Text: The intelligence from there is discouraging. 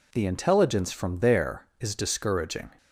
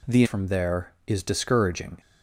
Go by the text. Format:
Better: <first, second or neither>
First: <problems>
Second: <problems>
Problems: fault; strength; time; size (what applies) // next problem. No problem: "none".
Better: first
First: none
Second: skips "intelligence"; at 0.2 s